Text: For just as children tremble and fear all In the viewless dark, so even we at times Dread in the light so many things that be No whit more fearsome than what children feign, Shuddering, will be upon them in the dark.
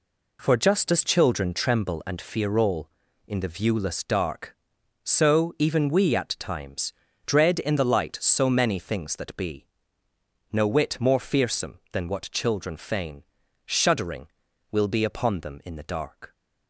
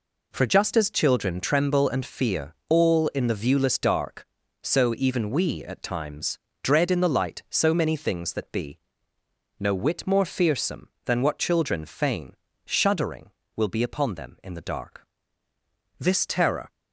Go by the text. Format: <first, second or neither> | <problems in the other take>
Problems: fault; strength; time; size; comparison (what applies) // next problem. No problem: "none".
first | pauses between "fear" and "all"; slight; at 2.5 s; 0.16 s long // pauses between "times" and "Dread"; slight; at 6.3 s; 0.26 s long; slight in the first // pauses between "be" and "No"; noticeable; at 8.7 s; 0.82 s long; noticeable in the first // goes on to say "This terror"; noticeable; from 15.9 s on; 0.74 s long